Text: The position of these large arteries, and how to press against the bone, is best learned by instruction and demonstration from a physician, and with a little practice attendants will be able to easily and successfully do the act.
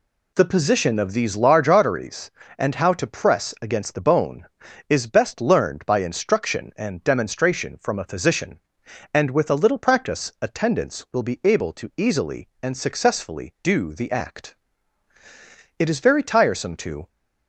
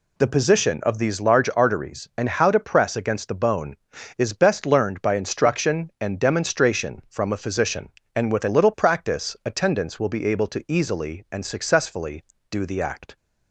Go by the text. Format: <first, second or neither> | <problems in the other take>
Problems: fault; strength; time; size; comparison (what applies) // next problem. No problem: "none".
second | goes on to say "It is very tiresome to"; noticeable; from 15.7 s on; 1.3 s long